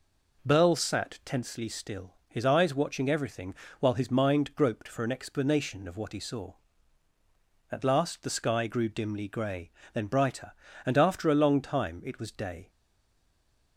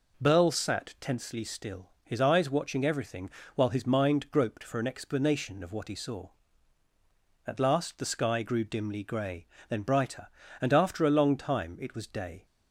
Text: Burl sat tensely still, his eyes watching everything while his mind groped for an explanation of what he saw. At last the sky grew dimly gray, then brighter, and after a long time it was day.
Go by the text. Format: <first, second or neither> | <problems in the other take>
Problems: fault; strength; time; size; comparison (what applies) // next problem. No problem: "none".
second | pauses between "everything" and "while"; slight; at 3.5 s; 0.26 s long; slight in the second // stays silent after the last word; from 12.6 s on; 1.1 s long